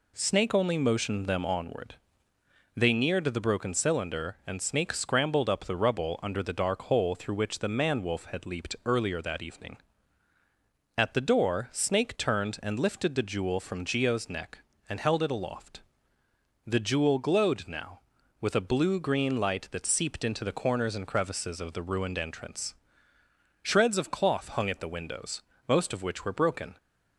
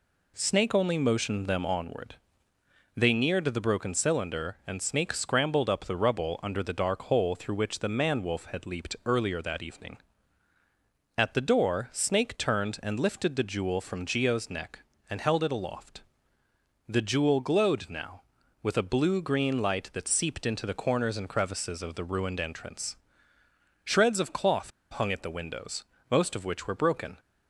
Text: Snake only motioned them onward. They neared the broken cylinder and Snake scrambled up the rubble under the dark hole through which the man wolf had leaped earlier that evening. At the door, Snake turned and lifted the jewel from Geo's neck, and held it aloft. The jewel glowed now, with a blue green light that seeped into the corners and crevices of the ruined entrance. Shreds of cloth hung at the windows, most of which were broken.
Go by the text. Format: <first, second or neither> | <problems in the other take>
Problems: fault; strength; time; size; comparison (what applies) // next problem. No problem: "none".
first | pauses between "cloth" and "hung"; slight; at 24.7 s; 0.20 s long